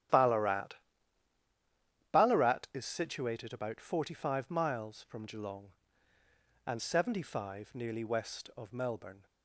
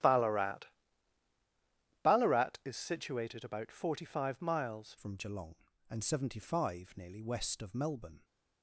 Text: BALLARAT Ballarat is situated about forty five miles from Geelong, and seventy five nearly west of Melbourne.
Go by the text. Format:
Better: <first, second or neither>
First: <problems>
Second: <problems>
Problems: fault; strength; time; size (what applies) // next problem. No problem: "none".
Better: first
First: starts louder than the rest; strong; until 2.4 s; 11 dB // pauses between "BALLARAT" and "Ballarat"; strong; at 0.7 s; 1.3 s long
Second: starts louder than the rest; strong; until 2.4 s; 11.5 dB // pauses between "BALLARAT" and "Ballarat"; strong; at 0.6 s; 1.3 s long // changes voice at "from"; from 4.9 s on; 3.3 s long